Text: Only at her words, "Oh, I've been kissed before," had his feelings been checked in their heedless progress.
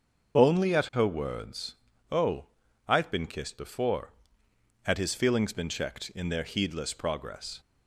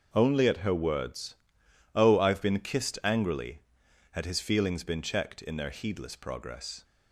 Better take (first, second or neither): first